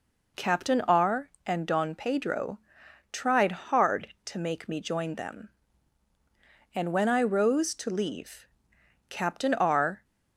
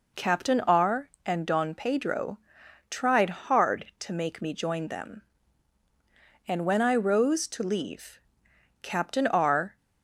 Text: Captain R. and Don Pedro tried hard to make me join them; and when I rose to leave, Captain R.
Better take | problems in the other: neither | pauses between "Pedro" and "tried"; noticeable; the same in both

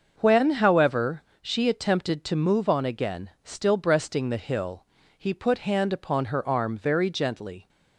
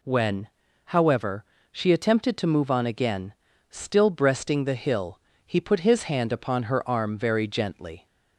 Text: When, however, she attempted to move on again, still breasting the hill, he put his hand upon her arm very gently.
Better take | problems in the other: second | starts louder than the rest; until 1.1 s; 6.5 dB // skips "his"; at 5.5 s

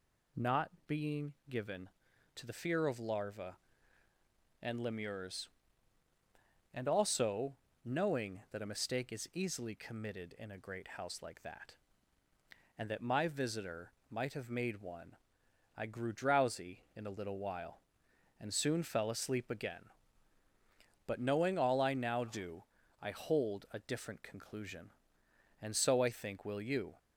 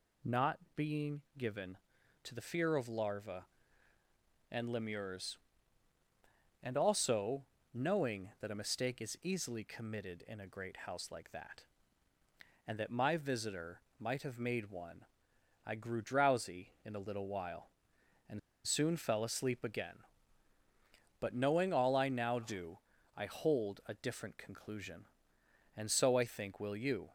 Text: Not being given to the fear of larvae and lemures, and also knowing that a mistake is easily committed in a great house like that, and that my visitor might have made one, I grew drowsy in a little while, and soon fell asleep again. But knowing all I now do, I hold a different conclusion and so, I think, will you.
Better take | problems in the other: first | pauses between "Not" and "being"; slight; at 0.5 s; 0.18 s long; slight in the first // pauses between "being" and "given"; slight; at 1.2 s; 0.16 s long; slight in the first // pauses between "also" and "knowing"; slight; at 7.4 s; 0.30 s long; slight in the first // pauses between "visitor" and "might"; slight; at 13.8 s; 0.18 s long; slight in the first // pauses between "and" and "soon"; slight; at 18.3 s; 0.25 s long

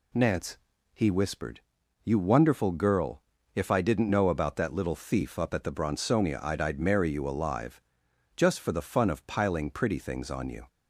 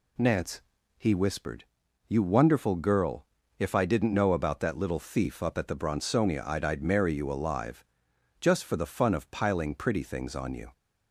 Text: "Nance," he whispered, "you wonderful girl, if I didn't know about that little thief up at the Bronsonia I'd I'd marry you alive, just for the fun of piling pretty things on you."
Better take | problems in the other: neither | none

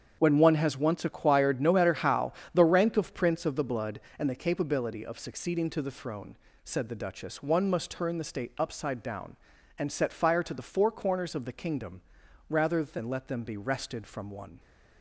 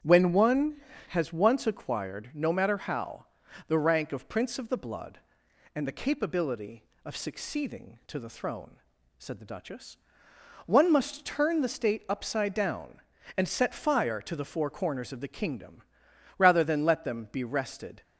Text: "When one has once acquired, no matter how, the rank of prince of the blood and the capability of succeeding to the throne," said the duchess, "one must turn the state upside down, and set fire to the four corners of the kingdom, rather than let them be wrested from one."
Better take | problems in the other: first | starts louder than the rest; strong; until 1.3 s; 8.5 dB; strong in the first // stops before "from one"; at 18.0 s

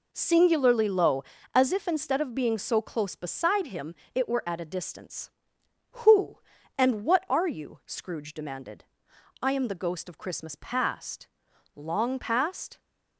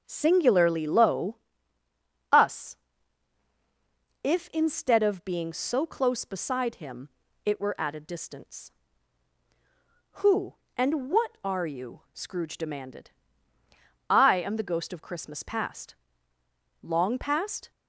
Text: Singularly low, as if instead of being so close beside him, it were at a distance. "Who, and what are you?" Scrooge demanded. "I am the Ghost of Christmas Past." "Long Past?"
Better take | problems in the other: first | starts louder than the rest; until 1.0 s; 7 dB // says "us" for "as"; at 2.3 s

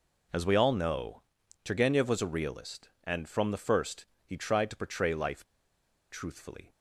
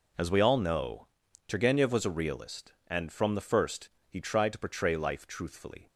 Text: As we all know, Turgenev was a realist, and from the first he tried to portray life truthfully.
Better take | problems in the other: second | pauses between "first" and "he"; slight; at 4.0 s; 0.18 s long; slight in the second // pauses between "life" and "truthfully"; noticeable; at 5.4 s; 0.65 s long

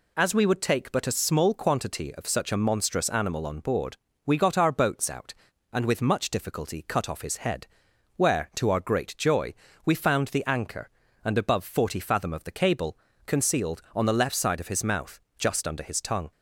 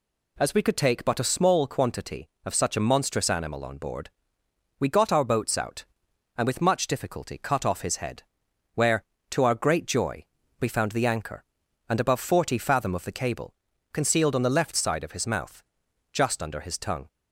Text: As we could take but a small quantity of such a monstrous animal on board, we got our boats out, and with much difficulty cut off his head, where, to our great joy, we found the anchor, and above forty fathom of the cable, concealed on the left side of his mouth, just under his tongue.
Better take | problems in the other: second | says "would" for "could"; at 0.4 s

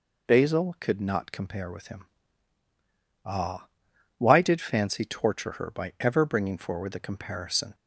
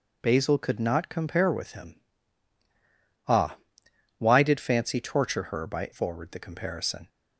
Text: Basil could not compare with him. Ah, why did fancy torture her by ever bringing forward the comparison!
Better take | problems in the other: first | skips "ever bringing"; at 5.9 s

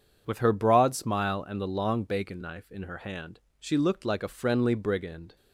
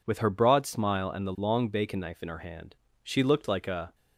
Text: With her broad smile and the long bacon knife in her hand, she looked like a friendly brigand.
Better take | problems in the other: first | stops before "friendly brigand"; at 3.9 s

